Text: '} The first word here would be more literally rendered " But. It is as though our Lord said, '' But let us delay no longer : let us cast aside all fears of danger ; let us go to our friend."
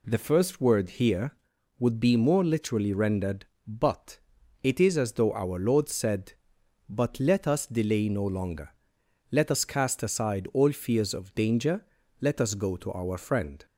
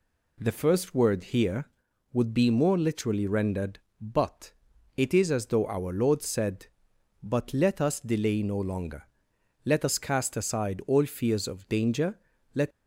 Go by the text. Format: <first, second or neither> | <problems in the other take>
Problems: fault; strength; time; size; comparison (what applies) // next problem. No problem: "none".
first | stops before "us go to our friend"; at 12.7 s